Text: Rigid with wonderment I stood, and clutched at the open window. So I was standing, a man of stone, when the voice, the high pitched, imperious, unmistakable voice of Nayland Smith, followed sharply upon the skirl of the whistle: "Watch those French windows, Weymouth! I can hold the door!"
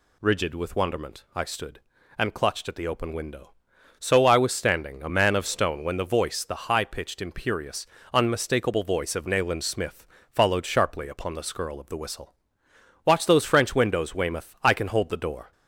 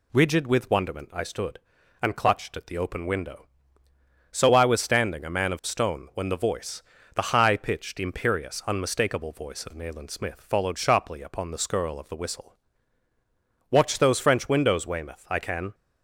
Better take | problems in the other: first | stops before "hold the door"; at 15.7 s

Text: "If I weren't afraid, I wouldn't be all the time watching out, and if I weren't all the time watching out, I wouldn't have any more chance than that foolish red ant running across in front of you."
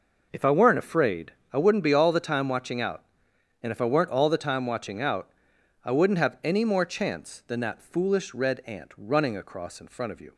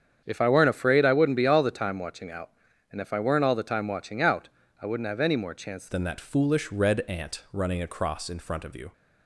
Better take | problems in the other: first | starts louder than the rest; strong; until 1.2 s; 8 dB // changes voice at "than"; from 5.8 s on; 3.1 s long

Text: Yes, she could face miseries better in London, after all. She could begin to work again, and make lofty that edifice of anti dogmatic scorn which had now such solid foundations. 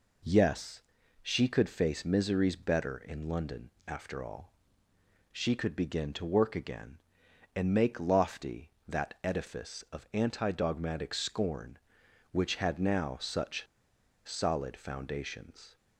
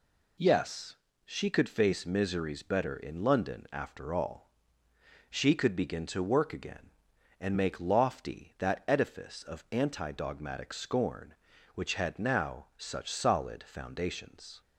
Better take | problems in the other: second | pauses between "such" and "solid"; noticeable; at 13.6 s; 0.63 s long

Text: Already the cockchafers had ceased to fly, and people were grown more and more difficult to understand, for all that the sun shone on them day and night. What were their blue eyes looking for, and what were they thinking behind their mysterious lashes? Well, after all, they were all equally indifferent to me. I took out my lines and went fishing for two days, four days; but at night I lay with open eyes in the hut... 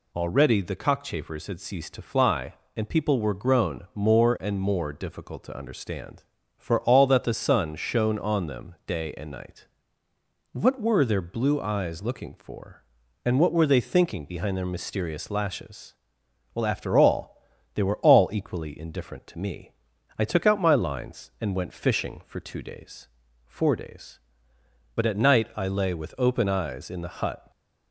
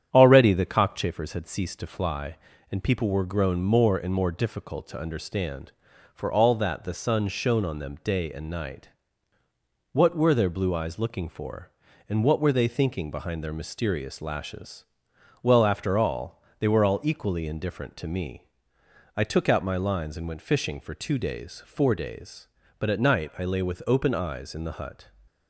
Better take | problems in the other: first | starts louder than the rest; strong; until 1.2 s; 9 dB

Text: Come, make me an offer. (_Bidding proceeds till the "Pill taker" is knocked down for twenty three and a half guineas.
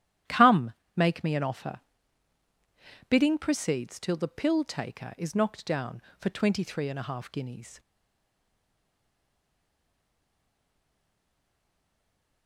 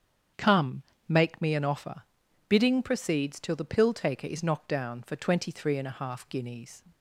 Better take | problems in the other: second | starts louder than the rest; strong; until 1.5 s; 11.5 dB; strong in the second // stays silent after the last word; strong; from 7.7 s on; 4.7 s long

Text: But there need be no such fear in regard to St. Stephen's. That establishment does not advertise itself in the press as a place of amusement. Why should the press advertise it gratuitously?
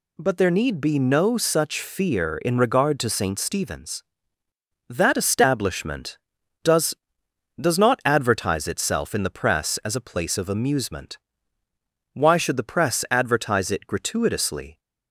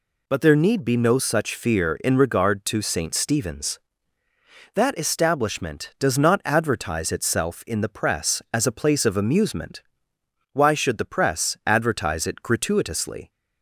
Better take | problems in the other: second | says "does" twice; at 7.6 s

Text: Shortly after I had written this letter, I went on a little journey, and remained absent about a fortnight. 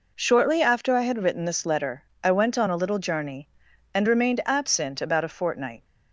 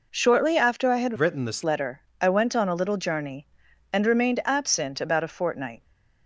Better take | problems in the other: first | changes voice from "written" to "this"; from 1.1 to 1.6 s; 0.5 s long

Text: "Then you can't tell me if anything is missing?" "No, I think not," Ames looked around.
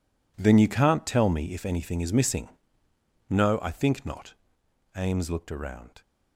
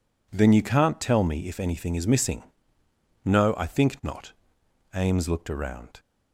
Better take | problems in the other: second | gets quieter; strong; throughout; 13.5 dB

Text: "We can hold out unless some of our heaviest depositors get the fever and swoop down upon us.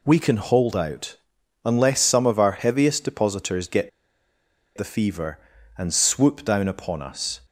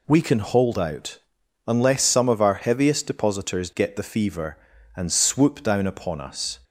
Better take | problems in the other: second | pauses between "out" and "unless"; noticeable; at 1.1 s; 0.48 s long; noticeable in the second // pauses between "get" and "the"; noticeable; at 3.8 s; 0.88 s long

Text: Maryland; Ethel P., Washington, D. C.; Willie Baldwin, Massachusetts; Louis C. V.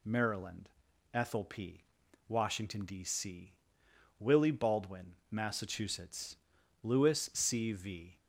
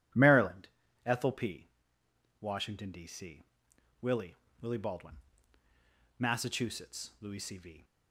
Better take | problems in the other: first | says "Willie" twice; at 4.6 s

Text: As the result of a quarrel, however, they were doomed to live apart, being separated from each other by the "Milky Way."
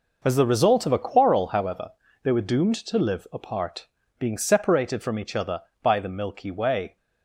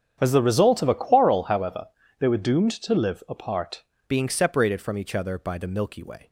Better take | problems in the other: first | starts louder than the rest; strong; until 1.2 s; 8.5 dB // changes voice at "being"; from 4.0 s on; 2.2 s long

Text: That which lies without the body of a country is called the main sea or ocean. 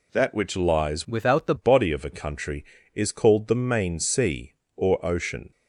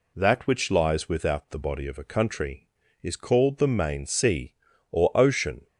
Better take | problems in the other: second | changes voice from "without" to "the"; from 1.0 to 1.5 s; 0.5 s long

